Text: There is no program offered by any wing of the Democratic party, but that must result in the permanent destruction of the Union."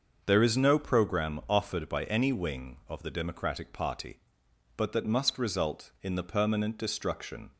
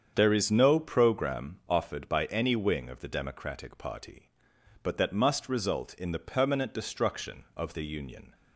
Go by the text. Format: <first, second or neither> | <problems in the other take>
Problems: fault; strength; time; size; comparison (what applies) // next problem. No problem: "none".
second | starts louder than the rest; until 1.2 s; 6.5 dB; strong in the second // stops before "of the Union"; at 7.5 s